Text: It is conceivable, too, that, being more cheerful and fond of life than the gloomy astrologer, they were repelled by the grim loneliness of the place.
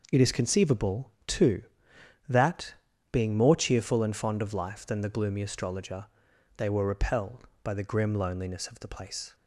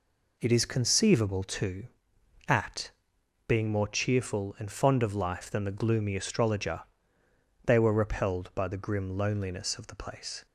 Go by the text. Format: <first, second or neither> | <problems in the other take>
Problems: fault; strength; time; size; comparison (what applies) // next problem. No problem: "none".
first | says "at" for "that"; at 2.4 s